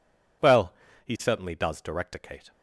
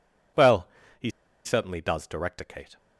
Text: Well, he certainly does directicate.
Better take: first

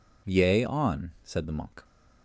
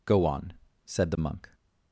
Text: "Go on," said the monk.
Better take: second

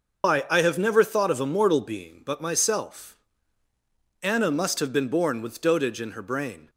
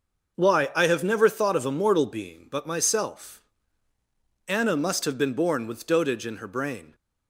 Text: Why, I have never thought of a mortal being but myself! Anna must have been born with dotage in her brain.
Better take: second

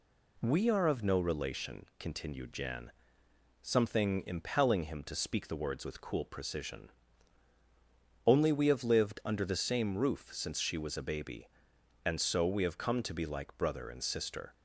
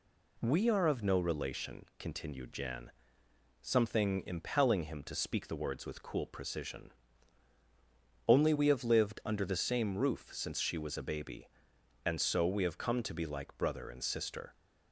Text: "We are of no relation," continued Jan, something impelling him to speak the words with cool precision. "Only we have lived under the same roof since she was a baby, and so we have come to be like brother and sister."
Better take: neither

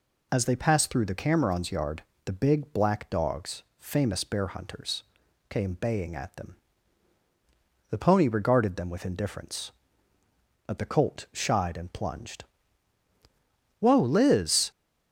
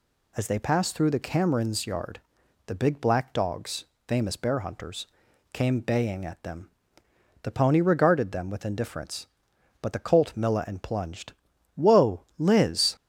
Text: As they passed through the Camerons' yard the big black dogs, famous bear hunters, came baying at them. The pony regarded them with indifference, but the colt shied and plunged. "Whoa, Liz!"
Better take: first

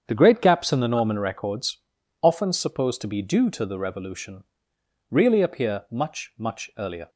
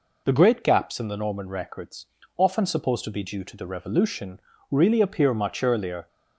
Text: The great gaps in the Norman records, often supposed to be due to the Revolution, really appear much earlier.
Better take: second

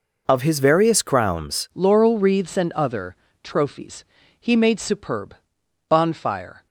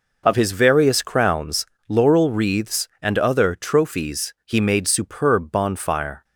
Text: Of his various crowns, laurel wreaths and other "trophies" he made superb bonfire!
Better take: second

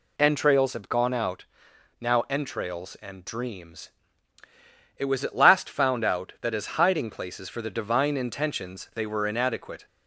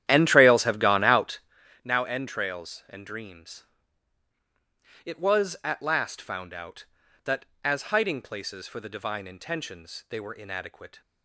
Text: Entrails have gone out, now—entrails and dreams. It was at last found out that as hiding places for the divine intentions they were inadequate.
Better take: first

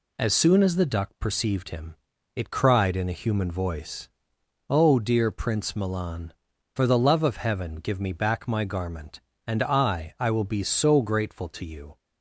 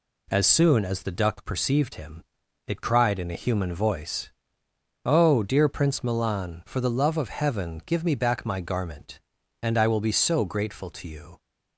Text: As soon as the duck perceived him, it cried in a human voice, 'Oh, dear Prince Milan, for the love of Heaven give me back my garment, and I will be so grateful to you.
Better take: second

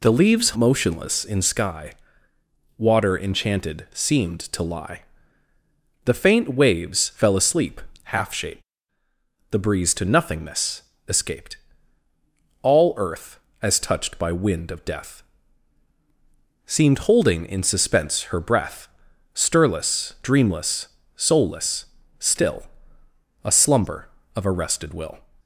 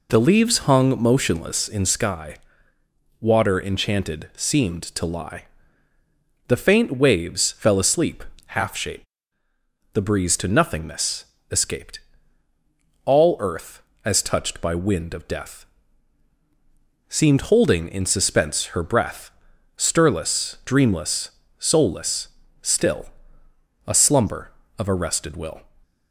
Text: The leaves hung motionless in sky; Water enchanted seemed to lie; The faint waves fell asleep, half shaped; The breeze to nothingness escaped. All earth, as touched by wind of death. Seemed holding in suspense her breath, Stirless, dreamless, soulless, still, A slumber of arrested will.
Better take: second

